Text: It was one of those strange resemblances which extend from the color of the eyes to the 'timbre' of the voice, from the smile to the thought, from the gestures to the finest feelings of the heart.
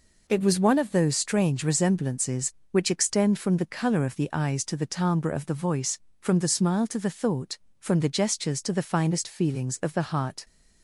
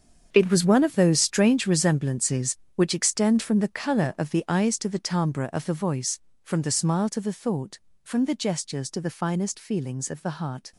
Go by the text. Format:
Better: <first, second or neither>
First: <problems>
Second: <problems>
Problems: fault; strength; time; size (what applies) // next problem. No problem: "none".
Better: first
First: none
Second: gets quieter; strong; throughout; 12.5 dB